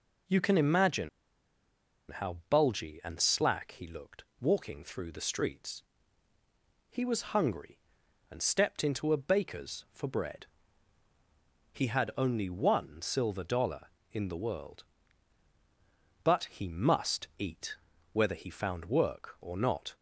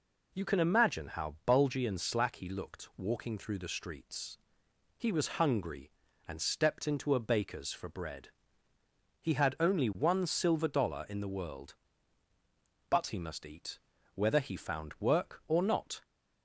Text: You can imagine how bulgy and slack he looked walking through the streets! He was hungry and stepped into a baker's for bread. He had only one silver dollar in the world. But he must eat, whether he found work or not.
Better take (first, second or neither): second